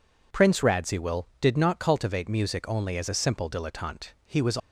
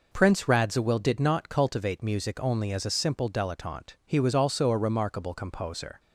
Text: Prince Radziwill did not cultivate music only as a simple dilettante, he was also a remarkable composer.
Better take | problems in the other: second | stops before "also a remarkable composer"; at 4.5 s

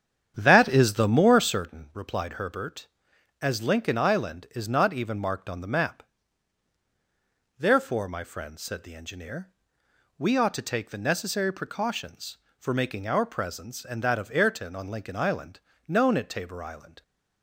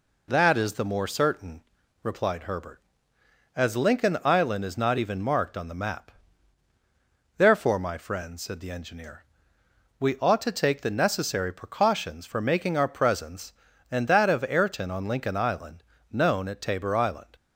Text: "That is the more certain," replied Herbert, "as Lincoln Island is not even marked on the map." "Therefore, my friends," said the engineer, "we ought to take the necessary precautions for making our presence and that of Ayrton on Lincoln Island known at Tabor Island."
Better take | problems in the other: second | starts louder than the rest; strong; until 1.7 s; 9 dB // pauses between "Island" and "known"; slight; at 15.6 s; 0.26 s long; slight in the second

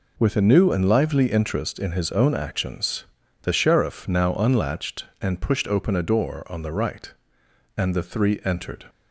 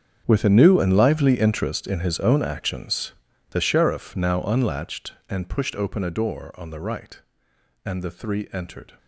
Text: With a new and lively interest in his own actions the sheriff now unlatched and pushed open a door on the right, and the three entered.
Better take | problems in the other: first | gets quieter; strong; throughout; 16 dB // pauses between "actions" and "the"; at 3.1 s; 0.38 s long; also in the first

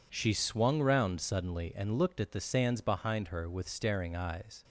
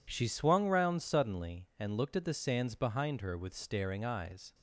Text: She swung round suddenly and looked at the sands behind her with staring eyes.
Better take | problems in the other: neither | none

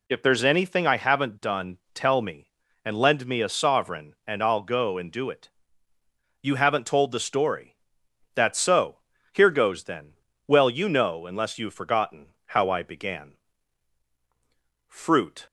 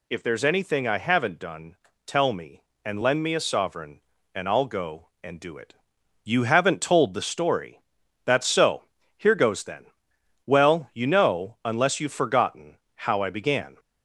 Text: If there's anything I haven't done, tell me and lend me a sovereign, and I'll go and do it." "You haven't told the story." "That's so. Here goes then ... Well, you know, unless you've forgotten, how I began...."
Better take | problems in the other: second | goes on to say "Fruit"; from 14.8 s on; 0.58 s long

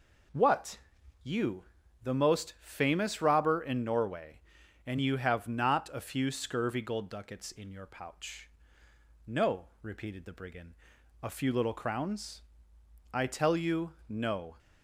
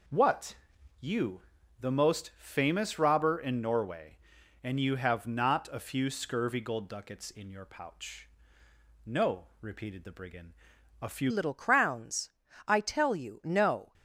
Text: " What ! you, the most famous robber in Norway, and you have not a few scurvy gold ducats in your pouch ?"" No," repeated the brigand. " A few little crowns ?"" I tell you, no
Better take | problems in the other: first | changes voice at "little"; from 11.2 s on; 2.7 s long

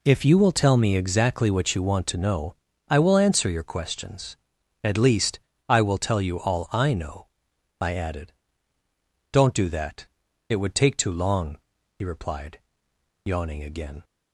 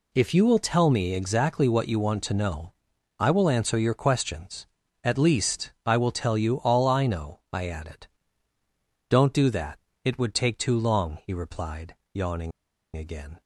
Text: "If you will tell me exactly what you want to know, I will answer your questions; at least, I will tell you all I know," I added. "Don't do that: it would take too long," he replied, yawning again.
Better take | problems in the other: first | pauses between "yawning" and "again"; at 12.5 s; 0.45 s long

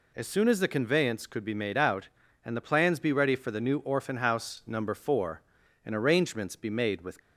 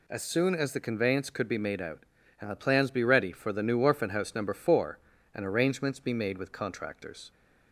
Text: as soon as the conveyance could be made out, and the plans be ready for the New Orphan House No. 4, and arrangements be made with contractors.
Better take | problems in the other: second | stops before "contractors"; at 7.2 s

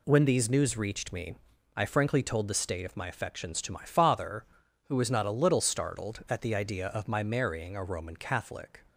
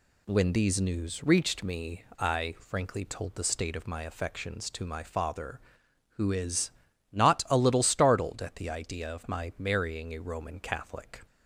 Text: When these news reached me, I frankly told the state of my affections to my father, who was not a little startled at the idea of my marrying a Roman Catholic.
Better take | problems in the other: first | says "is" for "was"; at 6.3 s

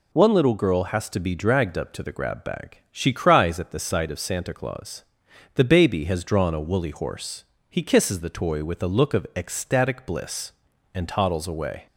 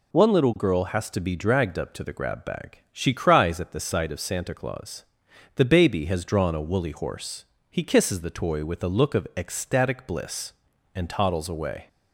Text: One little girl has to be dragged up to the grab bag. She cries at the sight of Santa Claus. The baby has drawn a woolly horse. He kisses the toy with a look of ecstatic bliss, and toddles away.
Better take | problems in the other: neither | none

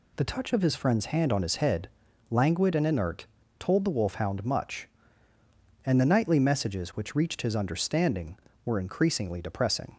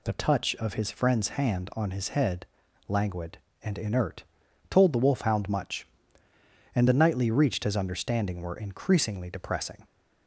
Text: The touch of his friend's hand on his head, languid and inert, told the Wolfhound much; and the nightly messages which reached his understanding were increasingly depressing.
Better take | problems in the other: first | skips "messages which"; at 7.2 s

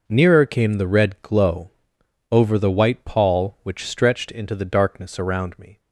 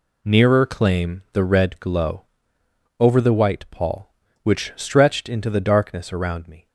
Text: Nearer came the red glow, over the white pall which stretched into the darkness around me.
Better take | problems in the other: first | says "claim" for "came"; at 0.6 s

